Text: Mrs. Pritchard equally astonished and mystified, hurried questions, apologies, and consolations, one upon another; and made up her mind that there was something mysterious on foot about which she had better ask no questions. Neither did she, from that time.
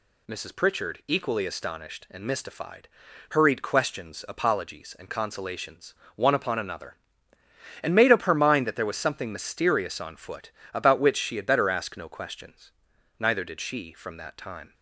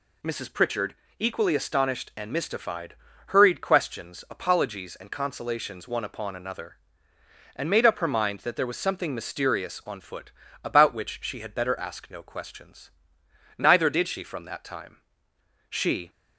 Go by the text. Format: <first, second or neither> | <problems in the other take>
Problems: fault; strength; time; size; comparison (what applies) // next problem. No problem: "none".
first | pauses between "Pritchard" and "equally"; slight; at 0.9 s; 0.24 s long // pauses between "foot" and "about"; slight; at 10.3 s; 0.32 s long; slight in the first // goes on to say "She"; slight; from 15.6 s on; 0.40 s long